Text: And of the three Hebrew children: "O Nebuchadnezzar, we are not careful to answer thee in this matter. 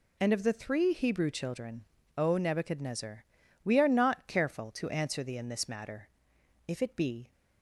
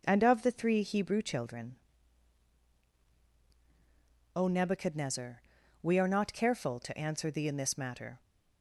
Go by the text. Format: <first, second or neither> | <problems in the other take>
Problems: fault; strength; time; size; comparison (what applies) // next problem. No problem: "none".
second | goes on to say "If it be"; noticeable; from 6.6 s on; 0.64 s long